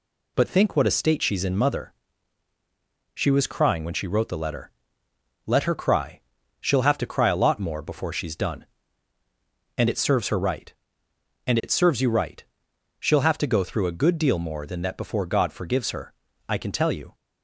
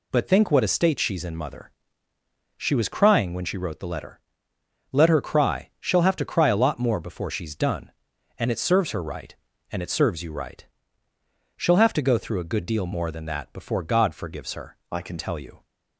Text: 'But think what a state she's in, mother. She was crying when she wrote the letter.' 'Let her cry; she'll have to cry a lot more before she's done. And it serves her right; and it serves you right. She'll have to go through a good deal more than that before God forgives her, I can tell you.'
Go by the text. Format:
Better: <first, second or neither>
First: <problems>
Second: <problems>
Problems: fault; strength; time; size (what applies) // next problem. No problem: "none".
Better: first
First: none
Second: changes voice from "I" to "can"; from 14.9 to 15.1 s; 0.2 s long